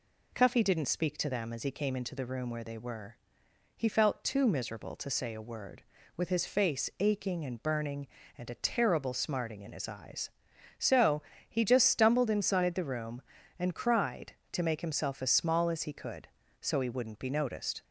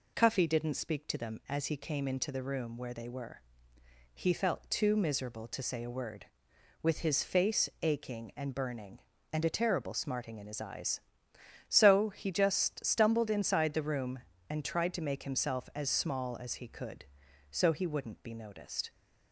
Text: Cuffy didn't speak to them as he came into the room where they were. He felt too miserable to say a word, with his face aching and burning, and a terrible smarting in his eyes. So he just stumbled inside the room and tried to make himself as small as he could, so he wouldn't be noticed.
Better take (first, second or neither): second